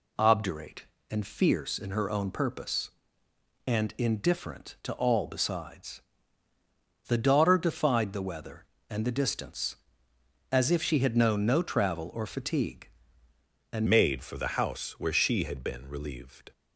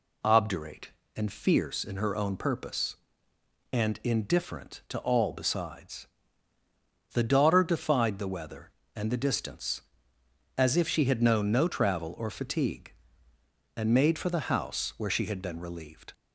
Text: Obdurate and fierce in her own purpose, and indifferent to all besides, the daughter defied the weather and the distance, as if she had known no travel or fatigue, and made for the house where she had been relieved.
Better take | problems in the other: second | changes voice at "made"; from 13.8 s on; 2.7 s long

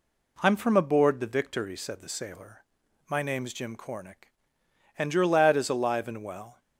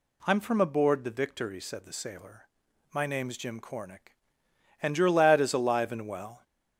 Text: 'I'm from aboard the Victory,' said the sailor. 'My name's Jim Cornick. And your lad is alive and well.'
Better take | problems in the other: first | gets louder; slight; throughout; 3 dB

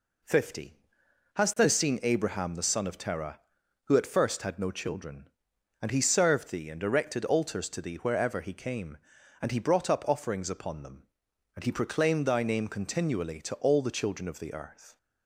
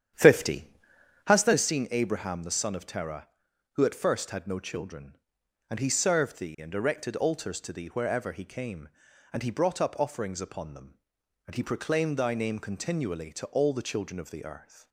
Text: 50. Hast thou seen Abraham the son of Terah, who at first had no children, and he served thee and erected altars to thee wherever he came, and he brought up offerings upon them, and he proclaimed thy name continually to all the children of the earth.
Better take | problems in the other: first | starts louder than the rest; strong; until 1.6 s; 9.5 dB

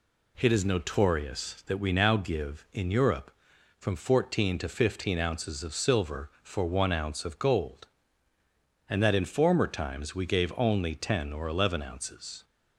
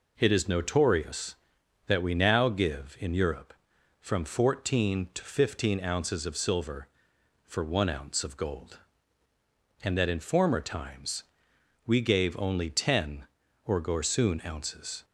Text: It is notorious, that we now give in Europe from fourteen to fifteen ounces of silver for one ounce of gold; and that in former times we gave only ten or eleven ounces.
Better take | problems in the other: first | pauses between "times" and "we"; noticeable; at 11.2 s; 0.60 s long // says "gorsoon" for "eleven"; at 13.7 s

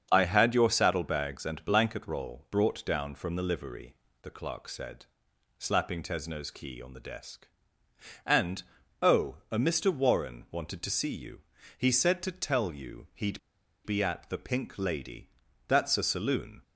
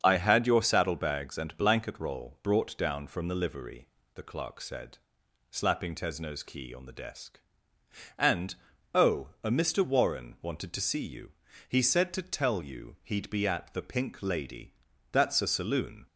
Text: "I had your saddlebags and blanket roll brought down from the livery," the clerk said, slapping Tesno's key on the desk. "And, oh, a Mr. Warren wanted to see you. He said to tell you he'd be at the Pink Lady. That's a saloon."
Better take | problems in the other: second | starts louder than the rest; until 1.1 s; 7 dB; also in the second // pauses between "he'd" and "be"; at 13.3 s; 0.45 s long

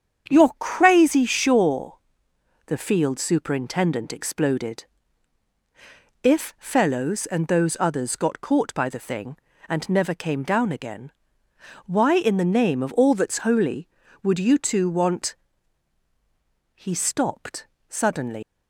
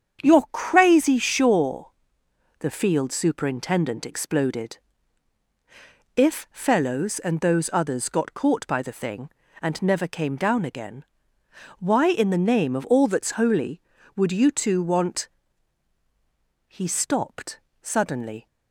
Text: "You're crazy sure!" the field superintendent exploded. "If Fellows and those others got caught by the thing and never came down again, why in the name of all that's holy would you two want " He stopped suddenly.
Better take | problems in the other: second | starts louder than the rest; strong; until 1.3 s; 8 dB; strong in the second // pauses between "stopped" and "suddenly"; slight; at 17.6 s; 0.22 s long; slight in the second // leaves "suddenly" unfinished; at 18.4 s; 100 ms

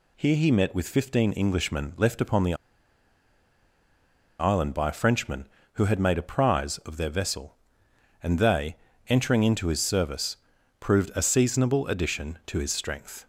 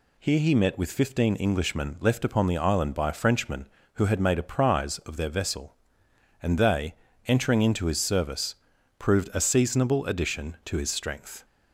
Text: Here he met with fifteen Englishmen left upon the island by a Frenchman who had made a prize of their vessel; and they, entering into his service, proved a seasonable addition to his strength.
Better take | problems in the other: second | pauses between "the" and "island"; strong; at 2.5 s; 1.8 s long

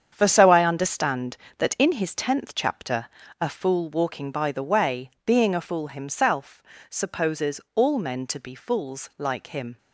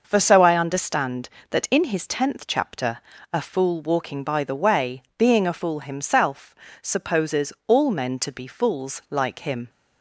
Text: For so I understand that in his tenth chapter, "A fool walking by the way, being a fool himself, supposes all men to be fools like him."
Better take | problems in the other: second | gets quieter; strong; throughout; 9 dB

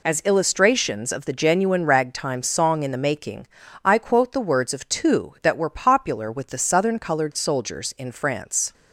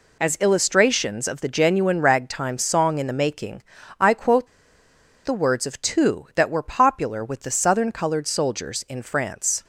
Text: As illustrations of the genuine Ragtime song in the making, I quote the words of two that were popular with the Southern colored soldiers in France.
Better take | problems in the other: first | pauses between "quote" and "the"; noticeable; at 4.4 s; 0.77 s long

